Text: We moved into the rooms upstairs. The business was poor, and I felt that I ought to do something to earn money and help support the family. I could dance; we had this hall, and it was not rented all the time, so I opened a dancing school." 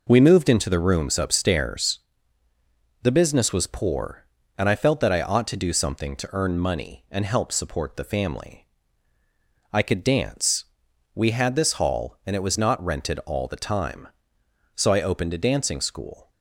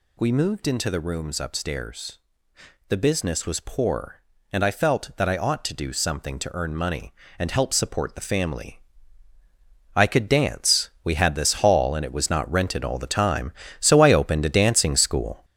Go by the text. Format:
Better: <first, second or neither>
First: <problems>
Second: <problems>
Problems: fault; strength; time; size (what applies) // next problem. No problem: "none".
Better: first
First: none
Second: gets louder; noticeable; throughout; 5.5 dB